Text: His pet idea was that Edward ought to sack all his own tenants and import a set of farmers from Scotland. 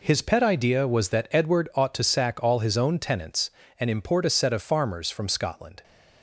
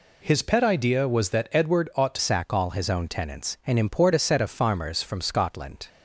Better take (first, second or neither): first